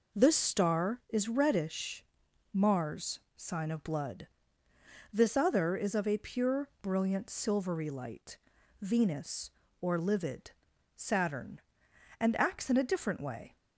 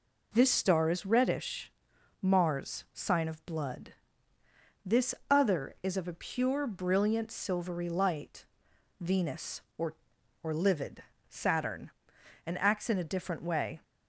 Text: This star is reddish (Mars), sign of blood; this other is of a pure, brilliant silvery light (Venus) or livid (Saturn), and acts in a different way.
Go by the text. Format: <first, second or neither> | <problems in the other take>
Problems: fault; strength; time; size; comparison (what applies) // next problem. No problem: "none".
first | pauses between "this" and "other"; slight; at 5.1 s; 0.16 s long // says "or" twice; at 10.4 s